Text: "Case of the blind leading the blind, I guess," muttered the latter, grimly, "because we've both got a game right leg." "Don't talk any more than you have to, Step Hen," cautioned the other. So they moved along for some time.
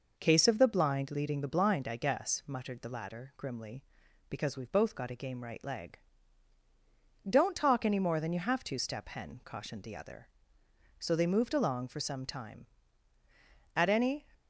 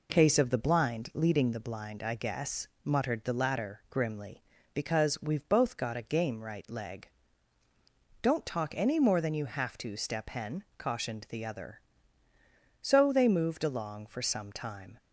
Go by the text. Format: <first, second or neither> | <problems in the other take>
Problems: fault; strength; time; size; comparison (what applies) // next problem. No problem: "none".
second | goes on to say "At any"; from 13.7 s on; 0.52 s long